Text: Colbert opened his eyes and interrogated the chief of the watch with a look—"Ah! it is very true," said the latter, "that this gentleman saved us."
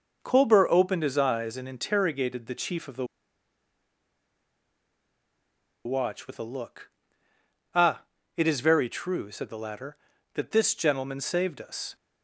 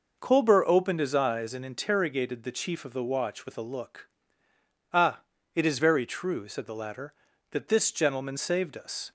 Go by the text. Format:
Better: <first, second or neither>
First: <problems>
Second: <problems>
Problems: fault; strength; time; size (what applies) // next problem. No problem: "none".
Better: second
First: starts louder than the rest; noticeable; until 1.2 s; 6 dB // pauses between "the" and "watch"; strong; at 3.0 s; 2.7 s long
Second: starts louder than the rest; noticeable; until 1.2 s; 6 dB